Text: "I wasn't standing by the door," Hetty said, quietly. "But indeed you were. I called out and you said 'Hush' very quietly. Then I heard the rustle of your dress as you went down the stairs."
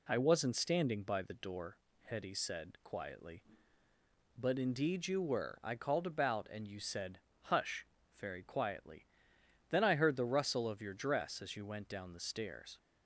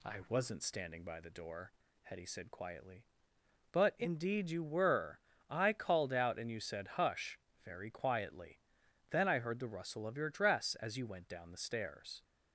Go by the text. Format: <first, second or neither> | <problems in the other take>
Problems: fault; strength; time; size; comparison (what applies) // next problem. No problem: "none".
second | says "about" for "out"; at 6.0 s // pauses between "said" and "Hush"; slight; at 7.1 s; 0.24 s long // pauses between "Hush" and "very"; slight; at 7.8 s; 0.30 s long; slight in the second